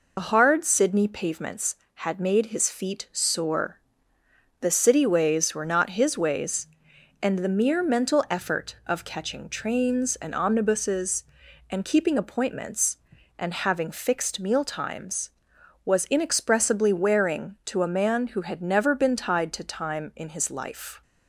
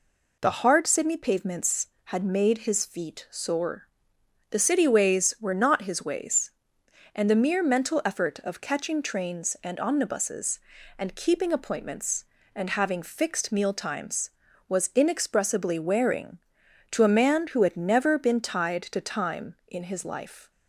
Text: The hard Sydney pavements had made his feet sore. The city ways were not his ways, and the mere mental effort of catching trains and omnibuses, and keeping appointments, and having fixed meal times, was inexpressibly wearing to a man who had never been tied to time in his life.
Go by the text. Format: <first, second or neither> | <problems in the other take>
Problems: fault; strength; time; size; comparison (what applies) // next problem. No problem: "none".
second | loses the start of "The"; at 0.1 s; 65 ms